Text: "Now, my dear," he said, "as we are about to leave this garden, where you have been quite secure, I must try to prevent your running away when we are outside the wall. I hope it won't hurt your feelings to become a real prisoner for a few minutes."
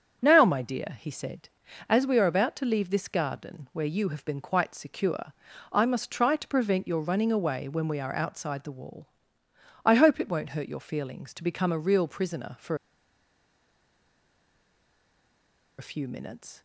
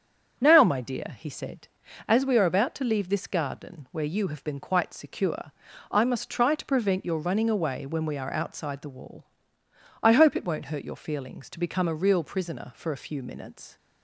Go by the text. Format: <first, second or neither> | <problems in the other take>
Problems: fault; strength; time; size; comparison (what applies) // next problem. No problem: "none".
second | starts louder than the rest; strong; until 1.2 s; 7.5 dB; strong in the second // pauses between "for" and "a"; strong; at 12.7 s; 3.0 s long